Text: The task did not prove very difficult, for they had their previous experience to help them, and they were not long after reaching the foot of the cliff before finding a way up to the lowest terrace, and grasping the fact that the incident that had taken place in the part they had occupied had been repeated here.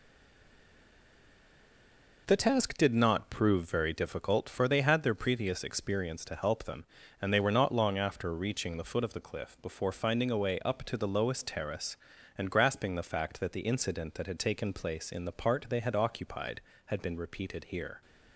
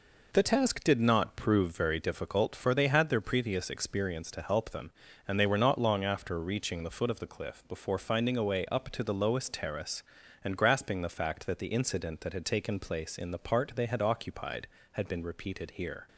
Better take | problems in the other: second | stays silent before the first word; until 2.2 s; 2.2 s long

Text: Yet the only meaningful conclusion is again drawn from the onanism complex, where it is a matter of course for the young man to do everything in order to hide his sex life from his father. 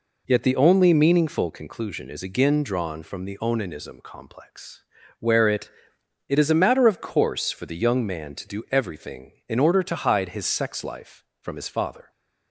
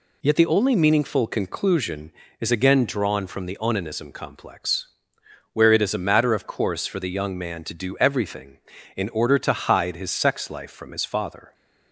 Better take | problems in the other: second | says "it" twice; at 6.2 s

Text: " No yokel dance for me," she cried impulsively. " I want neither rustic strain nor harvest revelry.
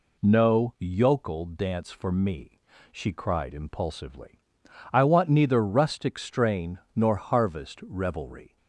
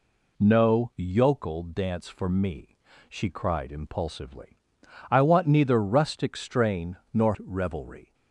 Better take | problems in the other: first | pauses between "strain" and "nor"; slight; at 6.9 s; 0.16 s long; slight in the first // skips "harvest"; at 7.3 s

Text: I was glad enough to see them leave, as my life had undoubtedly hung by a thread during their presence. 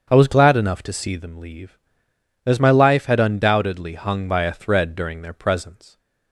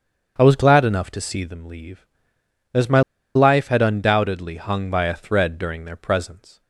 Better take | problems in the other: first | starts louder than the rest; until 1.4 s; 7 dB; also in the first // pauses between "my" and "life"; slight; at 3.0 s; 0.34 s long

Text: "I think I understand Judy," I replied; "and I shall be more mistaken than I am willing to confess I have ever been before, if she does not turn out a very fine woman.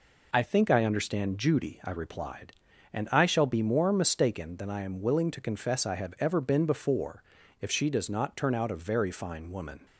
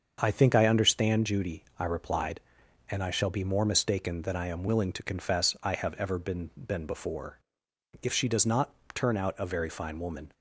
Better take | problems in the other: first | starts louder than the rest; until 1.2 s; 7 dB // says "been" twice; at 6.5 s // pauses between "not" and "turn"; slight; at 8.7 s; 0.20 s long

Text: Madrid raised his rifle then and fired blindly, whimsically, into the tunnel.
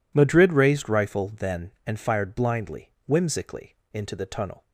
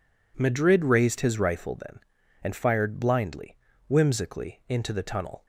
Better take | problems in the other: second | skips "his"; at 0.9 s

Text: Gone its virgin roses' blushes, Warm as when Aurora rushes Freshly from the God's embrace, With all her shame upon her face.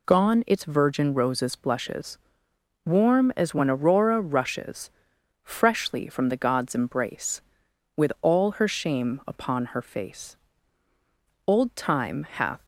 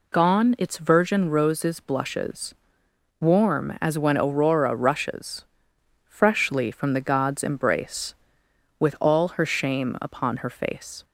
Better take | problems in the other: second | pauses between "rushes" and "Freshly"; noticeable; at 4.9 s; 0.52 s long; noticeable in the second // goes on to say "Old Time hath"; noticeable; from 11.4 s on; 1.1 s long

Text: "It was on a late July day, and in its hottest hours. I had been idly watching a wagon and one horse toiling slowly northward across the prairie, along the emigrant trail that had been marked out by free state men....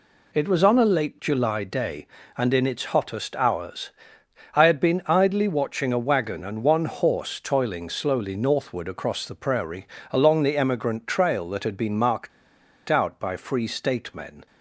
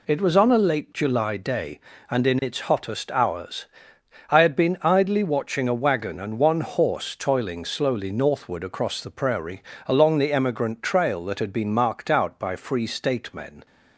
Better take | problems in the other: second | pauses between "marked" and "out"; noticeable; at 12.3 s; 0.59 s long

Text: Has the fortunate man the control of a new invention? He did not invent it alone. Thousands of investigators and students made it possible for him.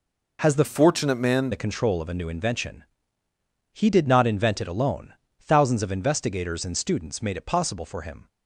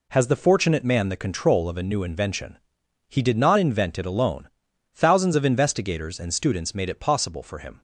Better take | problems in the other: second | changes voice from "fortunate" to "man"; from 0.6 to 1.5 s; 0.9 s long

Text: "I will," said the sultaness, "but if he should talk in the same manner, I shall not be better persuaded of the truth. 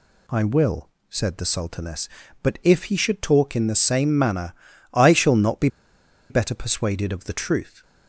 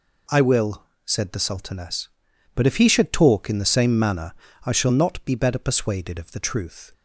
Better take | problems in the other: second | pauses between "be" and "better"; noticeable; at 5.6 s; 0.62 s long

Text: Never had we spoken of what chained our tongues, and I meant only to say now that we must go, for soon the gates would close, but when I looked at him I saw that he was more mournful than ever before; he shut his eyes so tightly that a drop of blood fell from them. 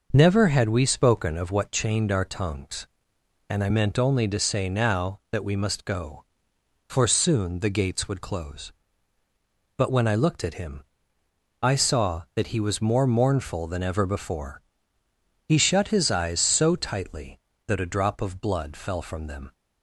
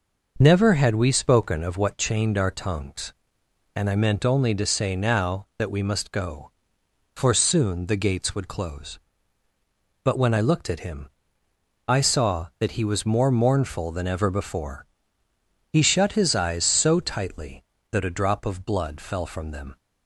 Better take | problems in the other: neither | pauses between "him" and "I"; noticeable; the same in both

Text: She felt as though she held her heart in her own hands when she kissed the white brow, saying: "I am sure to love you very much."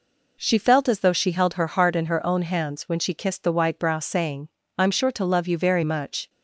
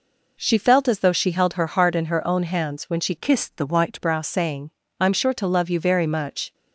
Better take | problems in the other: first | changes voice from "kissed" to "white"; from 3.1 to 4.0 s; 0.9 s long

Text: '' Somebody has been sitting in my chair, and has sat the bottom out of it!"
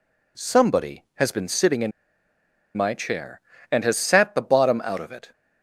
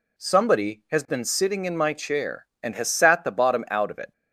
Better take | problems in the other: second | pauses between "in" and "my"; noticeable; at 1.9 s; 0.86 s long

